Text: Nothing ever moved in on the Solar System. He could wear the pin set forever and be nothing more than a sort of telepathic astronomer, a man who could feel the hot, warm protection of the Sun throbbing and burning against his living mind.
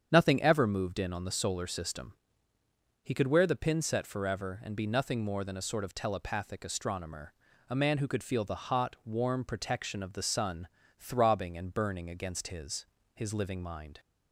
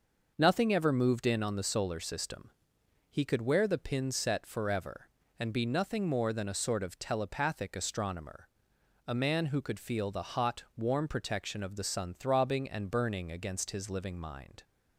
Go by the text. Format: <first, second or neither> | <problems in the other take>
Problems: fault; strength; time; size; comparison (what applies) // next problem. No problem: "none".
second | starts louder than the rest; strong; until 1.1 s; 8 dB; noticeable in the second // pauses between "Sun" and "throbbing"; slight; at 10.6 s; 0.32 s long // says "his" twice; at 13.1 s